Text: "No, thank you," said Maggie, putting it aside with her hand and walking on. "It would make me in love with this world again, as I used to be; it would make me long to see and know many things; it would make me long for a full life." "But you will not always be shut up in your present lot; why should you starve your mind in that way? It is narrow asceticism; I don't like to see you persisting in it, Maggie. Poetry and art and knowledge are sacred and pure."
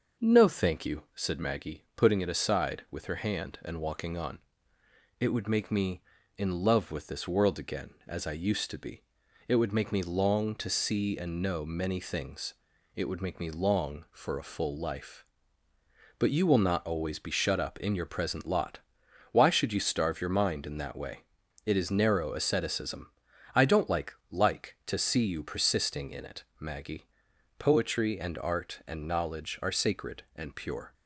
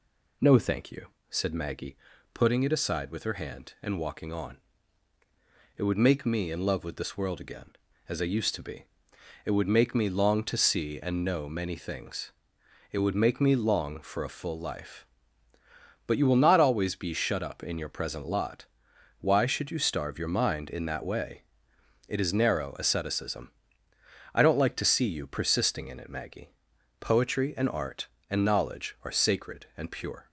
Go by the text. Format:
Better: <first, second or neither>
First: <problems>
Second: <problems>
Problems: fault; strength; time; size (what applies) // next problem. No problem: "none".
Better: second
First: starts louder than the rest; until 1.3 s; 6 dB // says "like" twice; at 24.3 s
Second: none